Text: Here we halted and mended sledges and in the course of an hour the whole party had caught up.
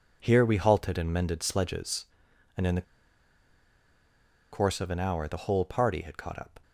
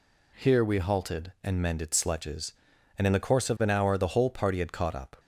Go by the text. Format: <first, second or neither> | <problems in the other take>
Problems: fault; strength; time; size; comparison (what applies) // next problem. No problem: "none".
second | pauses between "the" and "course"; strong; at 2.8 s; 1.7 s long